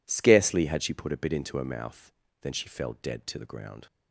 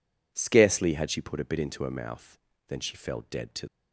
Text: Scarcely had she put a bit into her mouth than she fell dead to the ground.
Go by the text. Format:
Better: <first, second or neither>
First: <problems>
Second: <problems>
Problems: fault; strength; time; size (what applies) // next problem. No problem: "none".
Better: first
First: none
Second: stops before "the ground"; at 3.6 s